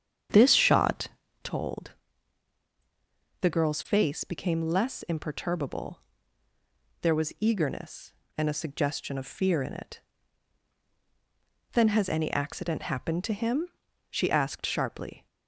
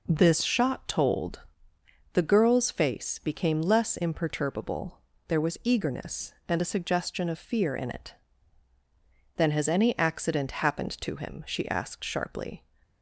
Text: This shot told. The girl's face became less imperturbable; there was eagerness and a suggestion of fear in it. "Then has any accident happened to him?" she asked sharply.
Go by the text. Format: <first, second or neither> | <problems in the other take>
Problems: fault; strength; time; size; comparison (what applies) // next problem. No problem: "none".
second | starts louder than the rest; strong; until 1.5 s; 8.5 dB // pauses between "shot" and "told"; slight; at 1.0 s; 0.34 s long